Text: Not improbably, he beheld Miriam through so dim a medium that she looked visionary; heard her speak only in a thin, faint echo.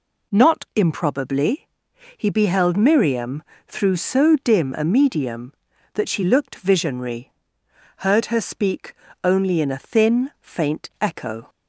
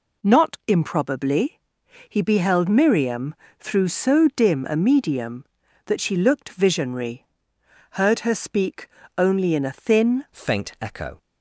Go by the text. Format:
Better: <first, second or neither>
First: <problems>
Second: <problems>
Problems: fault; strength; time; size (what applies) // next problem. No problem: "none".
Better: first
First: pauses between "Miriam" and "through"; slight; at 3.4 s; 0.24 s long // pauses between "speak" and "only"; slight; at 8.9 s; 0.28 s long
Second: pauses between "Miriam" and "through"; slight; at 3.3 s; 0.24 s long // pauses between "speak" and "only"; slight; at 8.8 s; 0.28 s long // changes voice at "faint"; from 10.3 s on; 0.9 s long